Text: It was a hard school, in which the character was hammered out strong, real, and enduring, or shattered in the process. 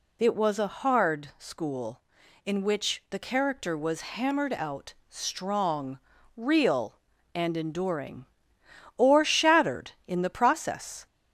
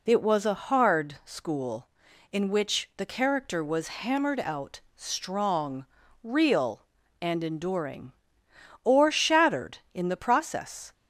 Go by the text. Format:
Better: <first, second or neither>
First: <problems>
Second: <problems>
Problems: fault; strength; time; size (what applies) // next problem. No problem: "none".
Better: second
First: gets louder; slight; throughout; 2.5 dB // pauses between "out" and "strong"; slight; at 4.9 s; 0.16 s long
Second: pauses between "out" and "strong"; slight; at 4.7 s; 0.16 s long